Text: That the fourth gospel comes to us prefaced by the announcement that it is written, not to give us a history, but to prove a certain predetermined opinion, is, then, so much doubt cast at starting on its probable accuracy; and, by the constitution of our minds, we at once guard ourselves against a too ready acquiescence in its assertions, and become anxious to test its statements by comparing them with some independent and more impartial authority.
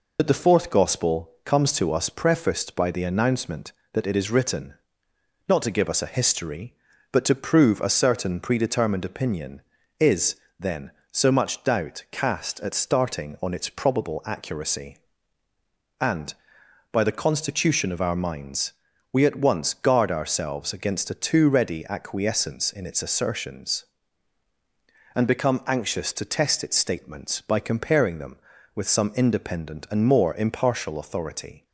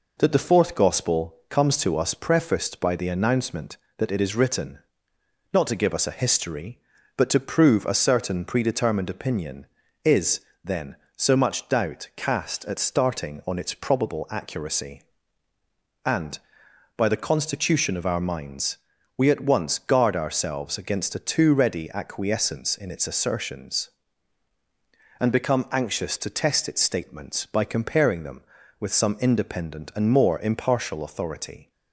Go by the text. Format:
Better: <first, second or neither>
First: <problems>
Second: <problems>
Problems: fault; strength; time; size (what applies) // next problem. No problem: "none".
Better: second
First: loses the start of "That"; at 0.1 s; 55 ms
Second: none